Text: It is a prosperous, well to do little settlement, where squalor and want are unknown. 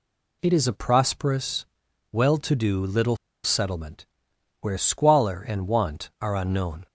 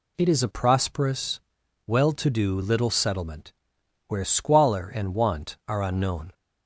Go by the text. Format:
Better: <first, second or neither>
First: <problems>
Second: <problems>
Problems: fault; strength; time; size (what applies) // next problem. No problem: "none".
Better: second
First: pauses between "little" and "settlement"; slight; at 3.1 s; 0.27 s long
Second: none